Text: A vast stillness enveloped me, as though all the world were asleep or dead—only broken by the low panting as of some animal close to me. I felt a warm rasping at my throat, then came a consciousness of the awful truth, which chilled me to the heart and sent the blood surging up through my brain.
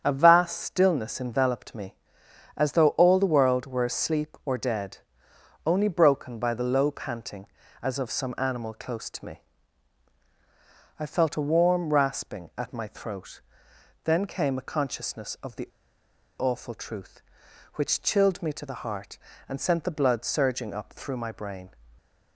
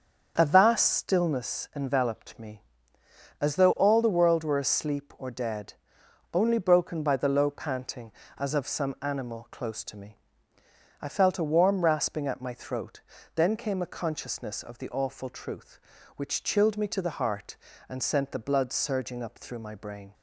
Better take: second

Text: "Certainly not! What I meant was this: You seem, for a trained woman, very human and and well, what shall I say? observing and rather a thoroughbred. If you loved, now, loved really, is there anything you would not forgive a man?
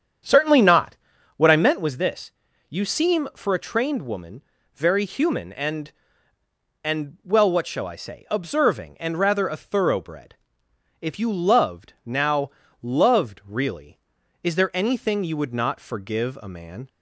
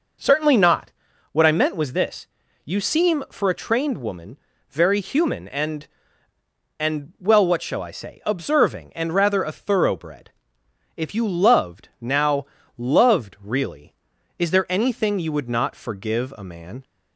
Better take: second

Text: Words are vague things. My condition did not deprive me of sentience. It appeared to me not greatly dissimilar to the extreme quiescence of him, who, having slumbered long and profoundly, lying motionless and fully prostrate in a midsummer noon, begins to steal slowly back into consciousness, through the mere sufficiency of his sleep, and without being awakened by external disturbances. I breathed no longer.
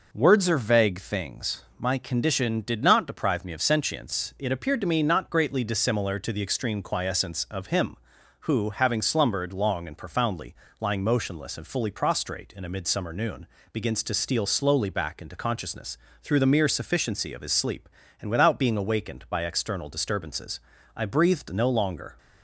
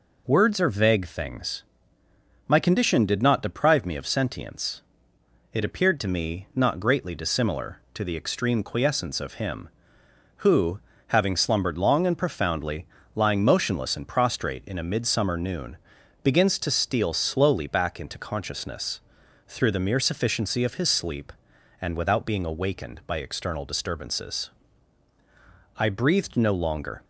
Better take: first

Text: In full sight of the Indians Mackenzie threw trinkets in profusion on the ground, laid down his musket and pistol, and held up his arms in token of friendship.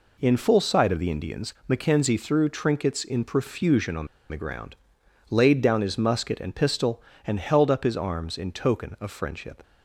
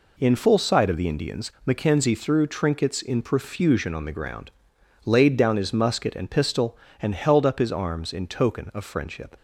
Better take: second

